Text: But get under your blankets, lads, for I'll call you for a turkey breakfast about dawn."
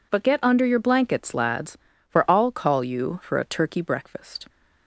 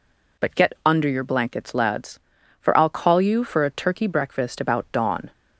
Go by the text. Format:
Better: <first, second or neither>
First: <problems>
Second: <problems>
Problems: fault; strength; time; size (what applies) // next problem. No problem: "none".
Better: second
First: stops before "about dawn"; at 4.4 s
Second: none